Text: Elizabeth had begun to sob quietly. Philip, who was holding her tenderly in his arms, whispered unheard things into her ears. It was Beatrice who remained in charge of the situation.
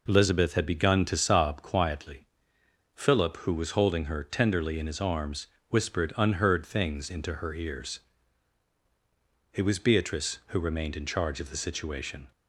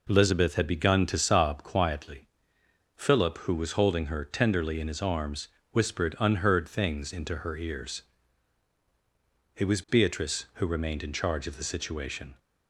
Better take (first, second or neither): neither